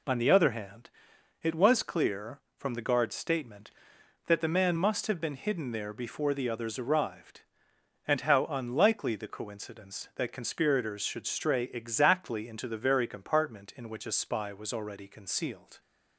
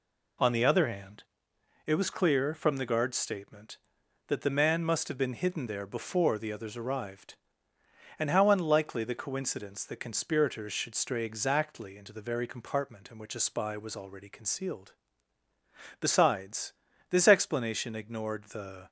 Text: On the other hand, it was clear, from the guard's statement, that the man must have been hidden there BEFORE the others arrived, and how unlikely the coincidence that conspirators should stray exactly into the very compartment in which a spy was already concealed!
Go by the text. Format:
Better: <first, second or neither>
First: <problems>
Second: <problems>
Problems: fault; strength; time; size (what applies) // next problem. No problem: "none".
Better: first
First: none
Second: goes on to say "Besides this explanation ignored the"; strong; from 16.0 s on; 2.8 s long